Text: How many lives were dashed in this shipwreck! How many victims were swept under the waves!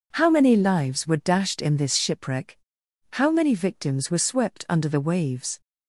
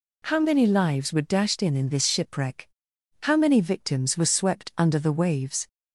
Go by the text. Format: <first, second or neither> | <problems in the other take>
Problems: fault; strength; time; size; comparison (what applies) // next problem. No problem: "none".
first | says "in" twice; at 1.7 s